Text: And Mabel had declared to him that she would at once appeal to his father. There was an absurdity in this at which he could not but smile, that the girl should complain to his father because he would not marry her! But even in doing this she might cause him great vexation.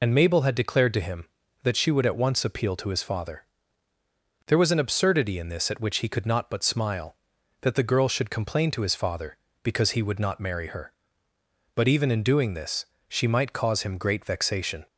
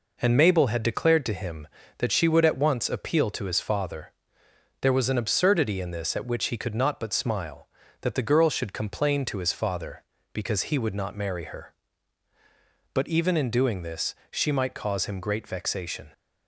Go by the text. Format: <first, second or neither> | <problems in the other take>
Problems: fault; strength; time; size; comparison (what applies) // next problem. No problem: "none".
second | loses the start of "And"; at 0.0 s; 35 ms // pauses between "this" and "she"; slight; at 12.8 s; 0.24 s long; slight in the second